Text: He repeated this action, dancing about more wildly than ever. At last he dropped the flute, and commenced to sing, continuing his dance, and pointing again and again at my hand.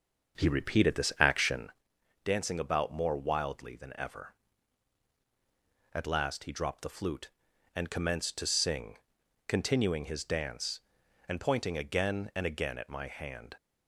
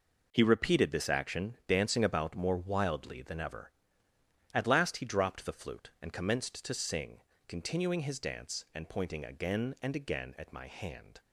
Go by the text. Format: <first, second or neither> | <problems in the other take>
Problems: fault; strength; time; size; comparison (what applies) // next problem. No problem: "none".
second | starts louder than the rest; until 1.8 s; 6.5 dB